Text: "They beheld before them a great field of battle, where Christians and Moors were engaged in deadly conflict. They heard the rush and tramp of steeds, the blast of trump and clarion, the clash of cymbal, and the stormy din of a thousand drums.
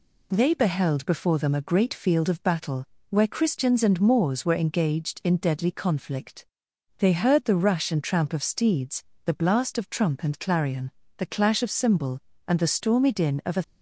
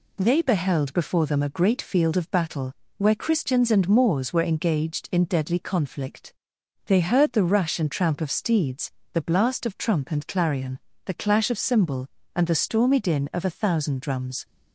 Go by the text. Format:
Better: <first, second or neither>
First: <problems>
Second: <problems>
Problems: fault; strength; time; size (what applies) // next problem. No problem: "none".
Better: second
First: stops before "thousand drums"; at 13.6 s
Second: none